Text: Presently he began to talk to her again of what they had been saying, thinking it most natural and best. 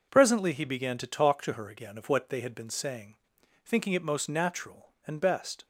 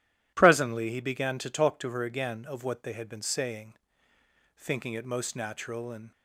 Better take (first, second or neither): first